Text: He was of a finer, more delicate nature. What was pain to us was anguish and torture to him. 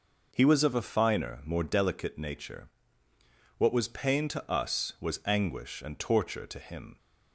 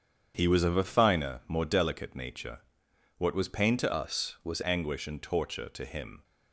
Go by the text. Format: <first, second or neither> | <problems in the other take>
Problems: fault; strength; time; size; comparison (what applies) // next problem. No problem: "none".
first | starts louder than the rest; strong; until 1.3 s; 8 dB // changes voice from "us" to "was"; from 3.9 to 4.6 s; 0.7 s long